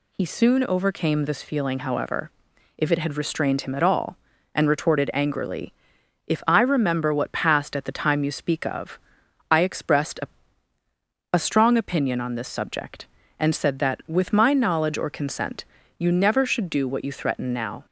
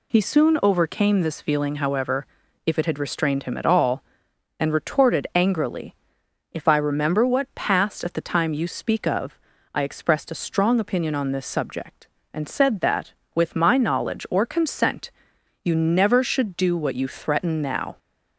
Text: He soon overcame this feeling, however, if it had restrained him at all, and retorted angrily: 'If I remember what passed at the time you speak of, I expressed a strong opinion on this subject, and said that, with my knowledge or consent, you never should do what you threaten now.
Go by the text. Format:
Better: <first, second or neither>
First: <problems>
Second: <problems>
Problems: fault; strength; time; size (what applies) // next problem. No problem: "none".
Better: second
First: says "a" twice; at 11.3 s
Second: none